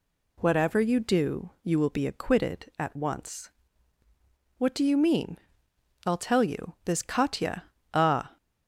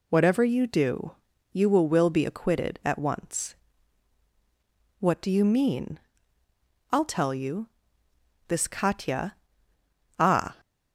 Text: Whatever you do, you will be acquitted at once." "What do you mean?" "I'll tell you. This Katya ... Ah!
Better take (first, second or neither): first